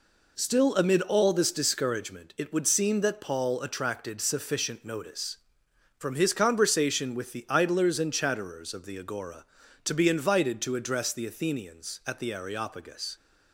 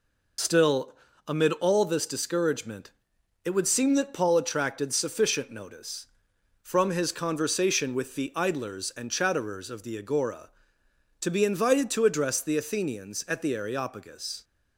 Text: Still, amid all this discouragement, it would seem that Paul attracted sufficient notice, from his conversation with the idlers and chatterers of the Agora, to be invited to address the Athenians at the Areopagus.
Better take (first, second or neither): first